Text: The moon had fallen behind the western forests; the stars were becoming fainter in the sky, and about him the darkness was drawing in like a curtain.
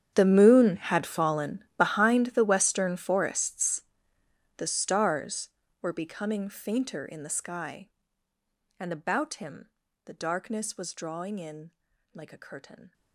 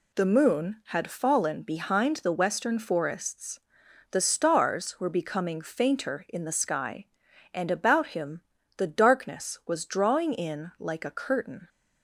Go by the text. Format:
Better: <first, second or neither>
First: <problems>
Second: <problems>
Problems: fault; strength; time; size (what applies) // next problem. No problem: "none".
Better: second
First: gets quieter; strong; throughout; 21.5 dB // pauses between "him" and "the"; slight; at 9.7 s; 0.34 s long // pauses between "in" and "like"; at 11.7 s; 0.40 s long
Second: pauses between "him" and "the"; slight; at 8.4 s; 0.34 s long